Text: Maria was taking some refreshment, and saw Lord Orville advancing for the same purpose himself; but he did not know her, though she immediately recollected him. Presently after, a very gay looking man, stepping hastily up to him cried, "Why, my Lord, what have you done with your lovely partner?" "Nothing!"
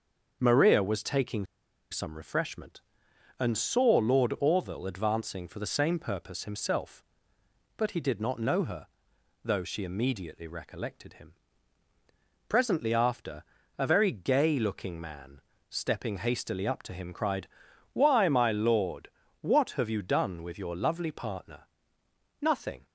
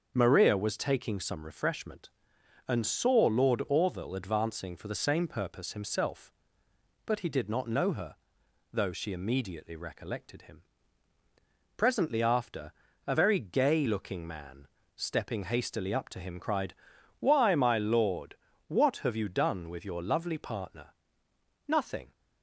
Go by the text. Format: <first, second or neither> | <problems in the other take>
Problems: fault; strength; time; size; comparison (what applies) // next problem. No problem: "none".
second | starts louder than the rest; until 1.4 s; 6.5 dB; also in the second // pauses between "taking" and "some"; at 1.4 s; 0.45 s long